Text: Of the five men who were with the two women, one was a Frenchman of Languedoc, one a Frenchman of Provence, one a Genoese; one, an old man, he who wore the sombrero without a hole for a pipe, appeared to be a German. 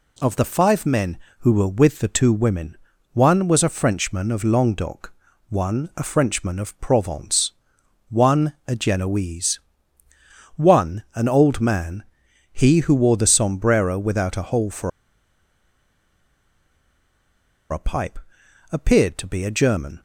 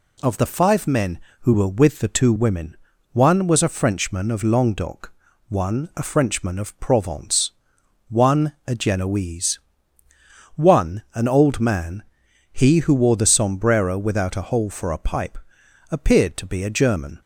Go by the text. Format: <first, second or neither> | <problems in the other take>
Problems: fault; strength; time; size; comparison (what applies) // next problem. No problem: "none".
second | pauses between "for" and "a"; strong; at 14.9 s; 2.8 s long